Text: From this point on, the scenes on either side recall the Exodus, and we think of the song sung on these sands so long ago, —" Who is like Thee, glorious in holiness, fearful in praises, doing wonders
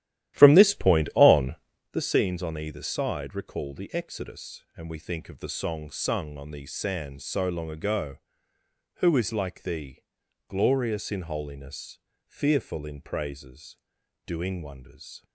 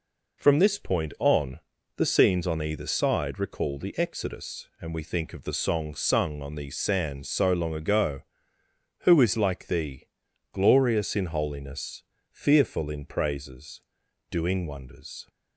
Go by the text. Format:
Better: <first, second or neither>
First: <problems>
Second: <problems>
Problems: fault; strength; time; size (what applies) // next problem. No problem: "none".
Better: second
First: starts louder than the rest; strong; until 1.9 s; 13.5 dB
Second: none